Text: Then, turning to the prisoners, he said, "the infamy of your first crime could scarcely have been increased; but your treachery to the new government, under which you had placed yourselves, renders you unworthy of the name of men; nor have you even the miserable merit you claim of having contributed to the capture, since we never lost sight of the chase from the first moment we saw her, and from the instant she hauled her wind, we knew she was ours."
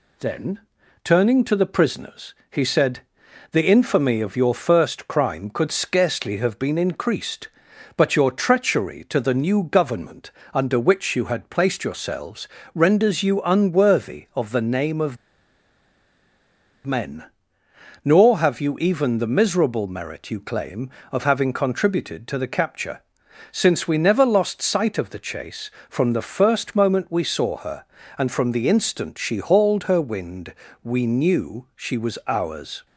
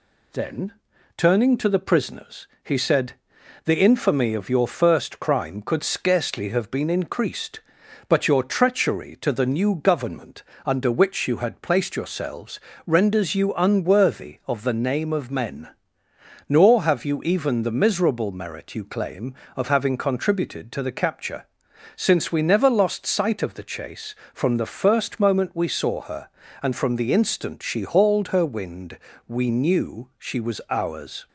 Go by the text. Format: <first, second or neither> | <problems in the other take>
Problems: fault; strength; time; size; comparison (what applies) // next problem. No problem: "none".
second | pauses between "of" and "men"; strong; at 15.1 s; 1.7 s long